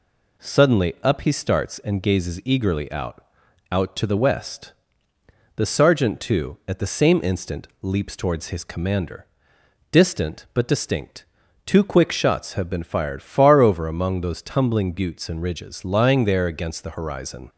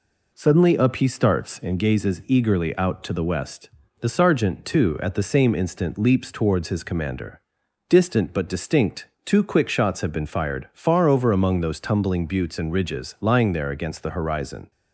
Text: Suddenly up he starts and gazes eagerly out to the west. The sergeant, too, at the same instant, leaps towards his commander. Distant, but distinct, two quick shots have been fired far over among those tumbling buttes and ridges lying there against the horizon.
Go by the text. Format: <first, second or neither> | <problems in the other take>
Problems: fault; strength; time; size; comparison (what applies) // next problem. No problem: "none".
second | says "out" twice; at 3.7 s